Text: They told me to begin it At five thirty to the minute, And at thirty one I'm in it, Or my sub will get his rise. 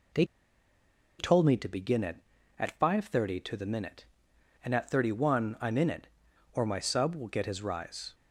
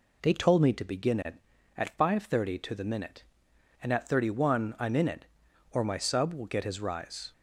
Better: second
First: pauses between "They" and "told"; noticeable; at 0.2 s; 0.94 s long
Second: none

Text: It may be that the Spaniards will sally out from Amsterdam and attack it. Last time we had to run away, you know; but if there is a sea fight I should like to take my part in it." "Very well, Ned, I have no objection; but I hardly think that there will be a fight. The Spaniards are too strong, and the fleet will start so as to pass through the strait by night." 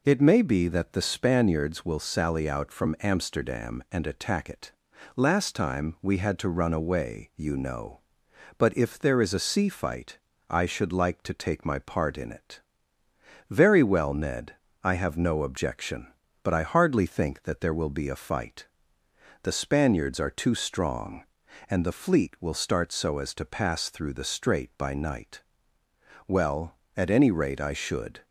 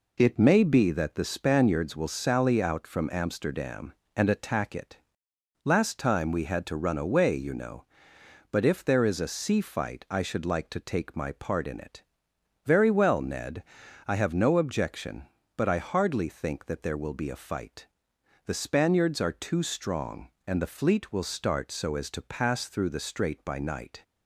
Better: second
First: pauses between "fight" and "I"; slight; at 10.1 s; 0.30 s long // goes on to say "Well at any rate I should"; strong; from 26.2 s on; 1.9 s long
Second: none

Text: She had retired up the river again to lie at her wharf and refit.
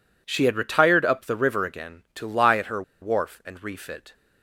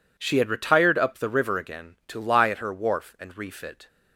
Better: second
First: pauses between "her" and "wharf"; slight; at 2.8 s; 0.19 s long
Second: none

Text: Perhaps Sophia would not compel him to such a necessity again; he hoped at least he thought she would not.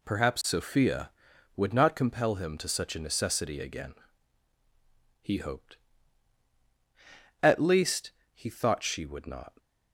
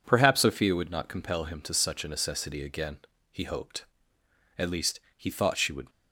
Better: first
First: pauses between "least" and "he"; slight; at 8.1 s; 0.24 s long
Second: pauses between "least" and "he"; slight; at 4.9 s; 0.18 s long // stops before "not"; at 5.8 s

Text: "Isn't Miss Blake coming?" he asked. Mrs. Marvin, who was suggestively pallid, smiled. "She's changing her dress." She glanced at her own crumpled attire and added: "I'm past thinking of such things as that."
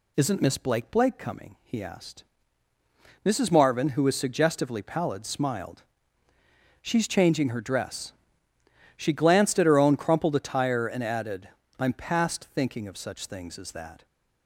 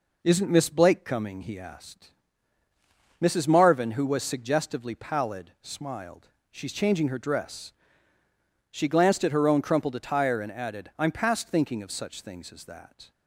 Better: second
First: says "Blake" twice; at 0.9 s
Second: none

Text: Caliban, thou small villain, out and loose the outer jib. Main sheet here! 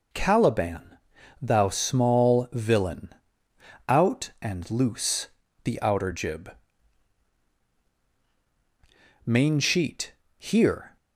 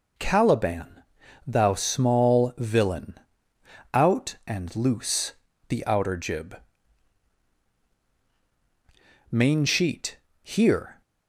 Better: neither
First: pauses between "loose" and "the"; slight; at 5.2 s; 0.36 s long // pauses between "sheet" and "here"; slight; at 10.1 s; 0.26 s long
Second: pauses between "loose" and "the"; slight; at 5.3 s; 0.35 s long // pauses between "sheet" and "here"; slight; at 10.1 s; 0.26 s long

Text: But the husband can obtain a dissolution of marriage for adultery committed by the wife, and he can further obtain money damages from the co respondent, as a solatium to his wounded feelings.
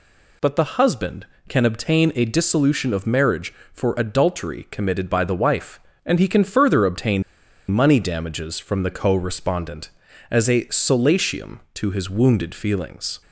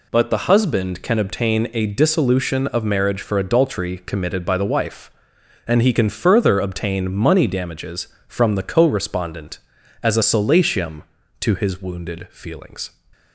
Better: second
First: pauses between "obtain" and "money"; noticeable; at 7.2 s; 0.48 s long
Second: none

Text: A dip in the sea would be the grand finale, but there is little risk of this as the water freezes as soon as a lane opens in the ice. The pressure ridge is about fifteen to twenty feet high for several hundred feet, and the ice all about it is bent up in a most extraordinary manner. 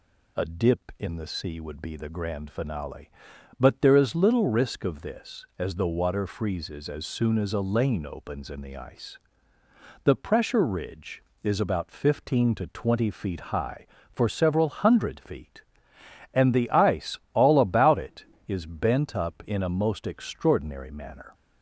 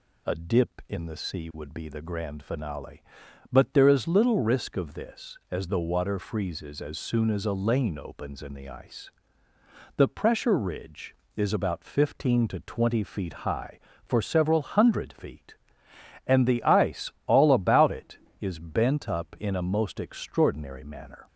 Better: neither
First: pauses between "ice" and "all"; slight; at 17.1 s; 0.16 s long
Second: pauses between "ice" and "all"; slight; at 17.1 s; 0.16 s long

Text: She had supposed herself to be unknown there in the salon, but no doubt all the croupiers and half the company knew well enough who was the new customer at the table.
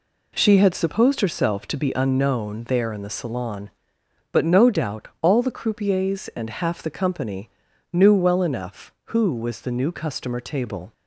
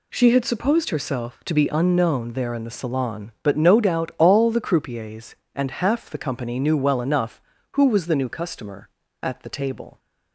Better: second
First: pauses between "company" and "knew"; at 7.5 s; 0.42 s long // skips "at the"; at 10.4 s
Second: none

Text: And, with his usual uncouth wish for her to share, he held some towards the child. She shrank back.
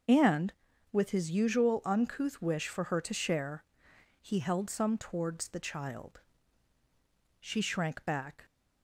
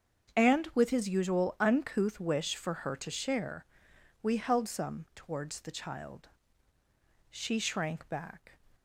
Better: first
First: starts louder than the rest; until 1.4 s; 6.5 dB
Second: starts louder than the rest; strong; until 1.4 s; 7.5 dB // says "we" for "he"; at 4.2 s

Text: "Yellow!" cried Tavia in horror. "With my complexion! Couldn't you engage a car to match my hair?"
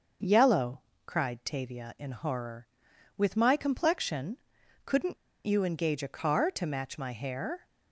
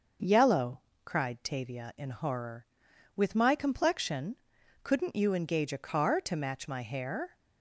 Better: second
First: starts louder than the rest; noticeable; until 1.5 s; 6 dB // pauses between "Couldn't" and "you"; slight; at 5.1 s; 0.29 s long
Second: starts louder than the rest; noticeable; until 1.4 s; 6 dB

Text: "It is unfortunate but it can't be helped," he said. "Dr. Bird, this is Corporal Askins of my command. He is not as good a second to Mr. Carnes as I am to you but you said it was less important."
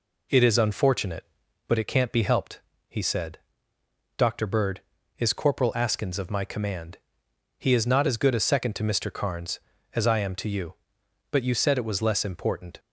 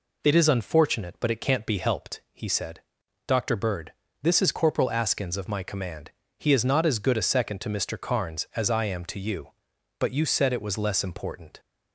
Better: second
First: skips "this"; at 4.9 s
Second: none

